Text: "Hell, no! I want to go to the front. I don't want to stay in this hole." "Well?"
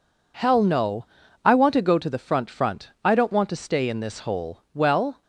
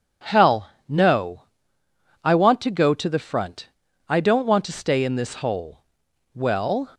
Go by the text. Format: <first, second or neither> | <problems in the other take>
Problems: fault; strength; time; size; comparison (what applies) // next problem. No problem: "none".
second | says "front" twice; at 2.4 s